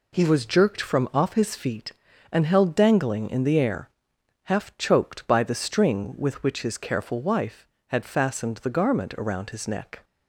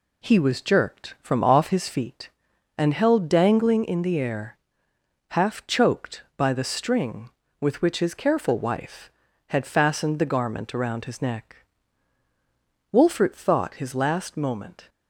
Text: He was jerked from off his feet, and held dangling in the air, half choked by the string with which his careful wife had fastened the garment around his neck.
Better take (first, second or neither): first